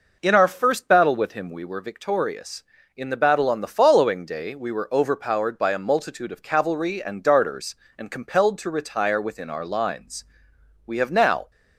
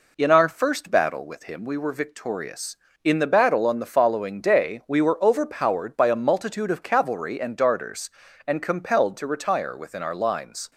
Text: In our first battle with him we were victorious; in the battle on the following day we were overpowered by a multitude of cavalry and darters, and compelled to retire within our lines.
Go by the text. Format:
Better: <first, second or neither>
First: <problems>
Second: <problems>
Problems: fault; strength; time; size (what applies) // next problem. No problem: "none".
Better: second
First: goes on to say "We have now"; noticeable; from 10.8 s on; 0.64 s long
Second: none